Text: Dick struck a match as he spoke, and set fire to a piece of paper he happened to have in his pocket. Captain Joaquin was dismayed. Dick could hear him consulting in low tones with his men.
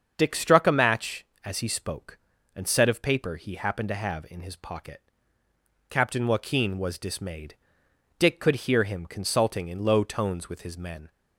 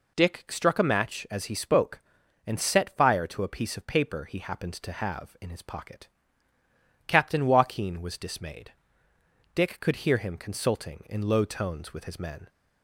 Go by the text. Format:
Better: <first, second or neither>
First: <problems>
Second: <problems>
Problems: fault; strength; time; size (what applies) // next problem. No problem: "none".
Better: second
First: starts louder than the rest; until 1.1 s; 7 dB // skips "fire to a piece"; at 2.8 s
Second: none